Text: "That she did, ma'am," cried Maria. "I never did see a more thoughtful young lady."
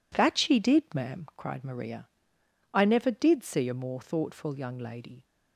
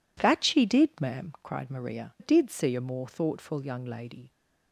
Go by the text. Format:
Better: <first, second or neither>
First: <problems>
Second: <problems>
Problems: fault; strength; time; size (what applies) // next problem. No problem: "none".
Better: first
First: none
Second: skips "I never"; at 2.1 s